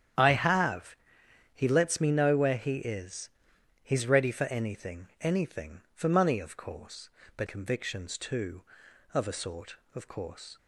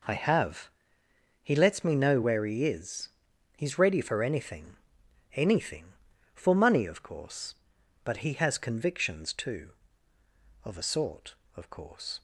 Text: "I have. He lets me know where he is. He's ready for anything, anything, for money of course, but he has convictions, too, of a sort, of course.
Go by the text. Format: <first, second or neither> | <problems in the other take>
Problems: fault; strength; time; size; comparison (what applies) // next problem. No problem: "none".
second | starts louder than the rest; strong; until 1.7 s; 9.5 dB // skips "he has"; at 7.4 s